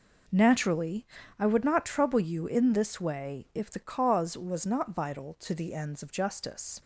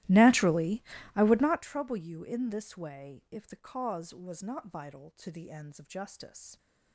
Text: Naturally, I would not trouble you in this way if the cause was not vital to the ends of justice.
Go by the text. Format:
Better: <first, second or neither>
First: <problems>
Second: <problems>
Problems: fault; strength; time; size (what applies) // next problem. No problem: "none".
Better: first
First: none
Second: starts louder than the rest; strong; until 1.6 s; 16 dB